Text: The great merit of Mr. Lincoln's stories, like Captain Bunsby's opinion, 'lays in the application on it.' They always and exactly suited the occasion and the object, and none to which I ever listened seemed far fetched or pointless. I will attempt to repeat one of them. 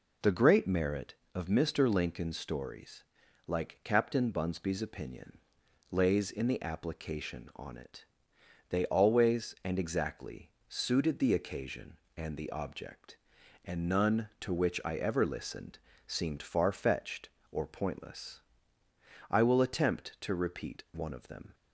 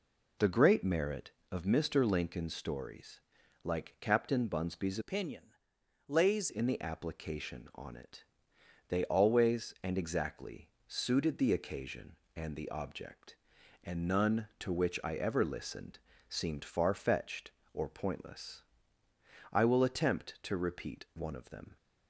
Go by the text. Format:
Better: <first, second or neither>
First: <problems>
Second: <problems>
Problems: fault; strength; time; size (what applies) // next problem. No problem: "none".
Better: first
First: pauses between "exactly" and "suited"; slight; at 10.5 s; 0.18 s long // pauses between "listened" and "seemed"; slight; at 15.7 s; 0.30 s long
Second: changes voice from "opinion" to "lays"; from 5.0 to 6.4 s; 1.4 s long // pauses between "exactly" and "suited"; slight; at 10.6 s; 0.18 s long // pauses between "listened" and "seemed"; slight; at 15.9 s; 0.32 s long